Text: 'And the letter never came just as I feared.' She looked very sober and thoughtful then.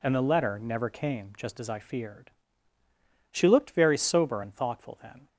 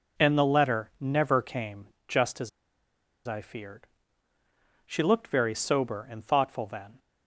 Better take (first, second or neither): first